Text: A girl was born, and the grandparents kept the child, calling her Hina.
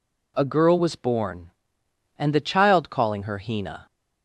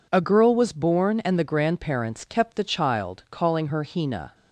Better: second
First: skips "the grandparents kept"; at 2.3 s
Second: none

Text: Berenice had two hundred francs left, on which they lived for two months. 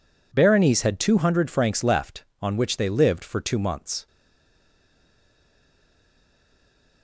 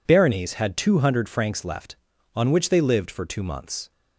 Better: second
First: stays silent after the last word; strong; from 4.0 s on; 3.0 s long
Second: none

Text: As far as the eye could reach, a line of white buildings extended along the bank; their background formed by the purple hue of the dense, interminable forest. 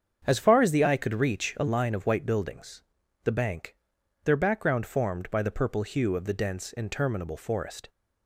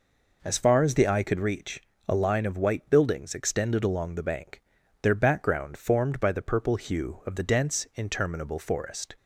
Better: second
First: starts louder than the rest; strong; until 1.2 s; 7.5 dB // skips "extended along"; at 3.0 s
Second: none

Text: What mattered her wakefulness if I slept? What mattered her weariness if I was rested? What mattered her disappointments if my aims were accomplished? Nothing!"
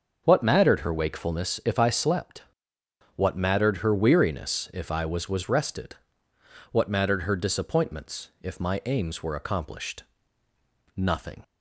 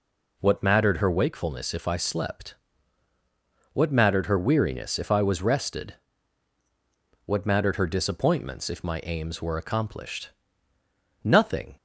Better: second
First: starts louder than the rest; until 1.2 s; 6.5 dB // says "was" twice; at 5.2 s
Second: none

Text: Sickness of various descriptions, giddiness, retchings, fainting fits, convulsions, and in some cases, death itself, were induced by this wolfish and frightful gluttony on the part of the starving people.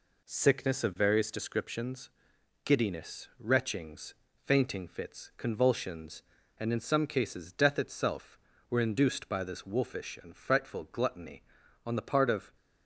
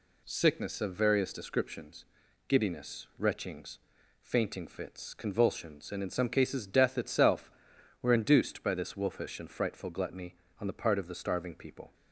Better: second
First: stops before "the starving people"; at 12.5 s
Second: none

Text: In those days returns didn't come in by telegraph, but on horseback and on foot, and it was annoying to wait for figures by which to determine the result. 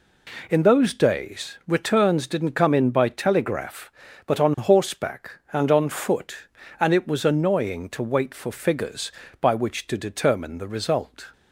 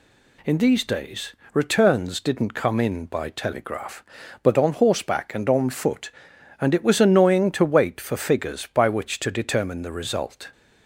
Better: first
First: none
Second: says "these" for "those"; at 0.5 s // pauses between "days" and "returns"; slight; at 1.3 s; 0.20 s long

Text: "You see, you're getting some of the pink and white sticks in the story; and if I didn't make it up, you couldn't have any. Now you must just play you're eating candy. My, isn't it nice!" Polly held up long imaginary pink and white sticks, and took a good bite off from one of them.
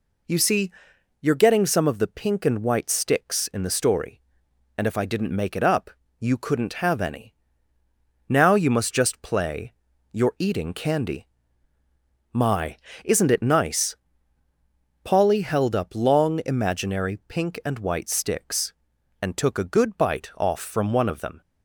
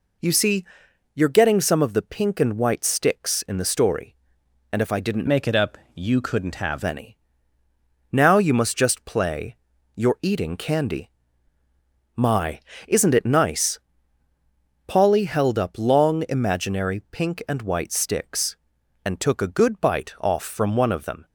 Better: first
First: pauses between "play" and "you're"; at 9.7 s; 0.40 s long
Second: changes voice from "make" to "have"; from 5.2 to 6.8 s; 1.6 s long // pauses between "play" and "you're"; at 9.5 s; 0.40 s long

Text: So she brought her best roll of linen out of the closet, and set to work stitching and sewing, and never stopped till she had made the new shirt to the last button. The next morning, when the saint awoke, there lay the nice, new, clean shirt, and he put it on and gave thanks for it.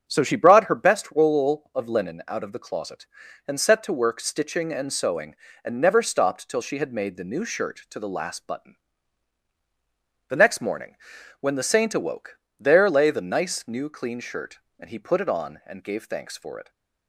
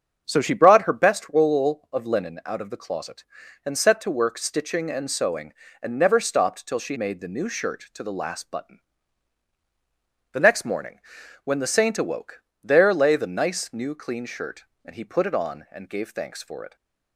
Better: first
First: starts louder than the rest; strong; until 1.0 s; 7 dB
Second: starts louder than the rest; strong; until 1.2 s; 7 dB // skips "had"; at 6.9 s

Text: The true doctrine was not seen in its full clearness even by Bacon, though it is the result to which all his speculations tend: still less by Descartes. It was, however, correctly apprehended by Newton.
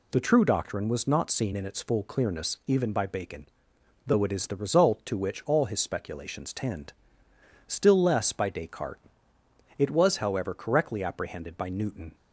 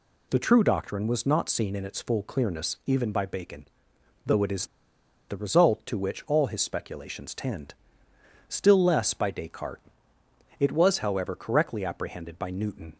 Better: first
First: none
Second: pauses between "is" and "the"; noticeable; at 4.6 s; 0.62 s long

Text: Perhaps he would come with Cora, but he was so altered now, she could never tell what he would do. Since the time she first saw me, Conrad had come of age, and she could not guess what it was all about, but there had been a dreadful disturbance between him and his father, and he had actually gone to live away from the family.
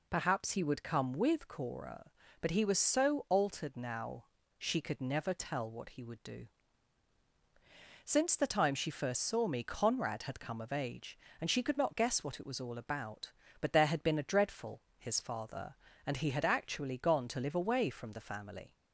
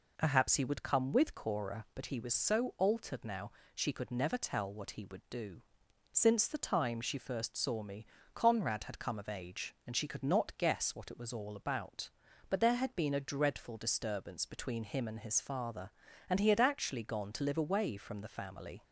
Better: second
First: skips "disturbance between him and"; at 14.8 s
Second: none

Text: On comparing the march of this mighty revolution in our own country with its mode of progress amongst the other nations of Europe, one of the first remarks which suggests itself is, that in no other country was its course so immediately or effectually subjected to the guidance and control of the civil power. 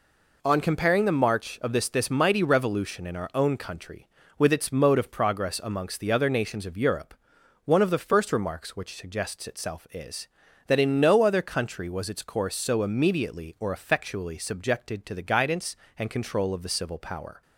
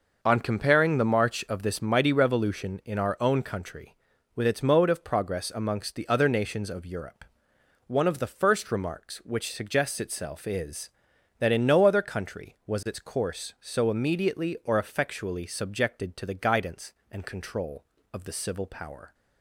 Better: second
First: says "this" twice; at 1.8 s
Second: none

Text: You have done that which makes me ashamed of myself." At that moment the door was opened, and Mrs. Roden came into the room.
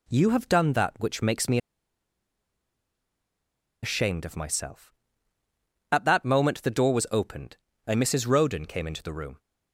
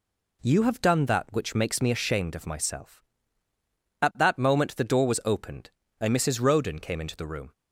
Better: second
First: pauses between "me" and "ashamed"; strong; at 1.5 s; 2.2 s long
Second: none

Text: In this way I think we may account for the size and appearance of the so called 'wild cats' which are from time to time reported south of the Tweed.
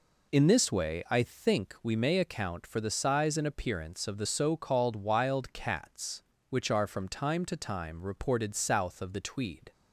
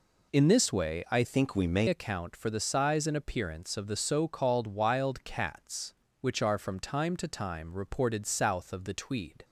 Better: first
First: none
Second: changes voice from "think" to "may"; from 1.2 to 1.8 s; 0.6 s long

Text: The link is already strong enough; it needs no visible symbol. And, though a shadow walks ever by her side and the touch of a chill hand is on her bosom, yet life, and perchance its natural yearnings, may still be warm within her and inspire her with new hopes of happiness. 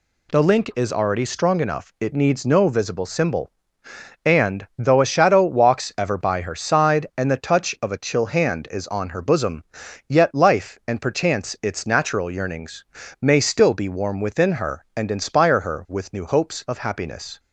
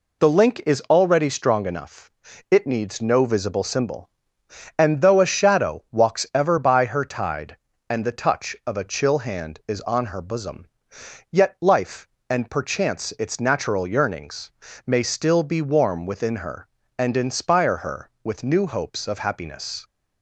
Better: first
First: none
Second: says "tide" for "side"; at 7.0 s

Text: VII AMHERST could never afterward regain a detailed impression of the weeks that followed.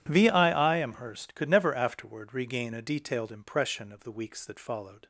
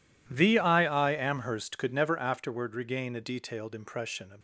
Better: first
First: none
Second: stops before "the weeks that followed"; at 4.3 s

